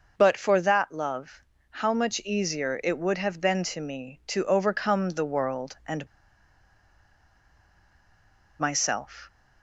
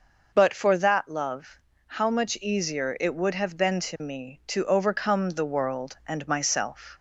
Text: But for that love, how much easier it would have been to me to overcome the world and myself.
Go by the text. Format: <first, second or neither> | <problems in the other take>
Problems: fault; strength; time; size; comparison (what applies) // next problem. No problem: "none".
second | pauses between "and" and "myself"; strong; at 6.0 s; 2.5 s long